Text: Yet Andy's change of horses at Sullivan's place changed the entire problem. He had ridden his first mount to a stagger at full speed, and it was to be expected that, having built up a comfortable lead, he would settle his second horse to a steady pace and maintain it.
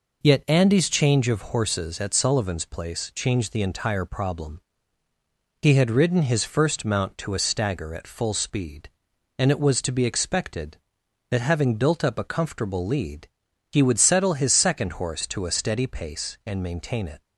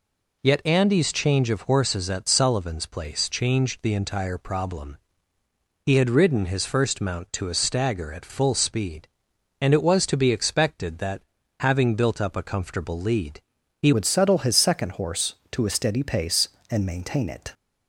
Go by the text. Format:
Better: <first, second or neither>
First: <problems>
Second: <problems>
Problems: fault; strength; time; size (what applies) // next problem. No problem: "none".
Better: first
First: none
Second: changes voice at "would"; from 13.9 s on; 3.6 s long